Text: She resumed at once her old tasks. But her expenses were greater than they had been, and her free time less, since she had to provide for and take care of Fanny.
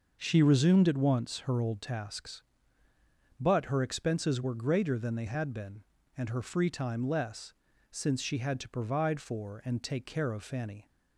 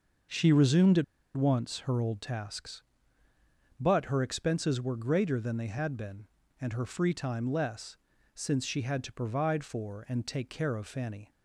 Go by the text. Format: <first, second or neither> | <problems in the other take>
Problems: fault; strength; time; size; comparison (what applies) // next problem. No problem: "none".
first | pauses between "at" and "once"; slight; at 1.0 s; 0.33 s long